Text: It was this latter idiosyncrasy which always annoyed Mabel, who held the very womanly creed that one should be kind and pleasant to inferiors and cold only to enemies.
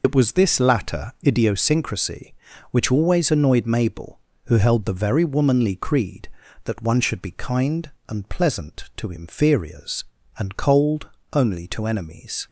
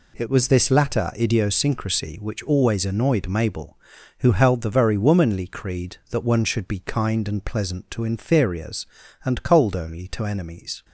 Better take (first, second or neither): second